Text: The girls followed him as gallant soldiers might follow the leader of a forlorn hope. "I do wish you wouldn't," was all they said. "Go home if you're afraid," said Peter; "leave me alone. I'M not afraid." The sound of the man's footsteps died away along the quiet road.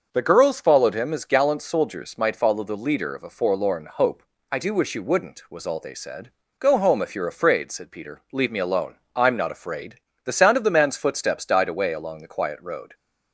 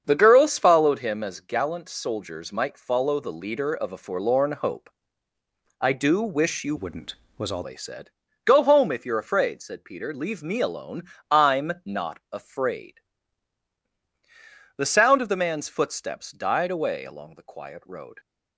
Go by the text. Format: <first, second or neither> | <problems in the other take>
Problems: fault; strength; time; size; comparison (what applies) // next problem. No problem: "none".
first | starts louder than the rest; strong; until 1.0 s; 7 dB; also in the first // changes voice from "wouldn't" to "all"; from 6.7 to 7.6 s; 0.9 s long